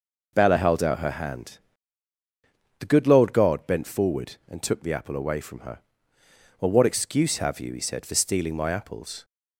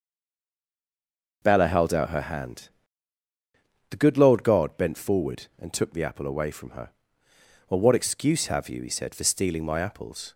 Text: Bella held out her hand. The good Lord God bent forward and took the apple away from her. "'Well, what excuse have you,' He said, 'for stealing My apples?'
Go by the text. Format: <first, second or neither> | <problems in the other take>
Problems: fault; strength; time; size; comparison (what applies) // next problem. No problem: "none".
first | stays silent before the first word; noticeable; until 1.4 s; 1.4 s long